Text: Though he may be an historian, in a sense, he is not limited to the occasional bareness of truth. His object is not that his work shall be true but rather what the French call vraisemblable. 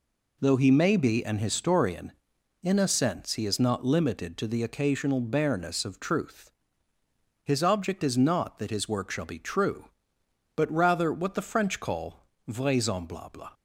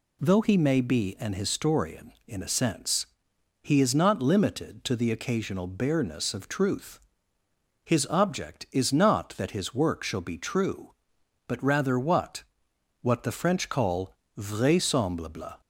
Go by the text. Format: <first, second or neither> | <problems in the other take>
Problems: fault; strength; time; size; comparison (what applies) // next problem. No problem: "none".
first | says "what" twice; at 13.0 s // pauses between "call" and "vraisemblable"; slight; at 14.1 s; 0.24 s long; slight in the first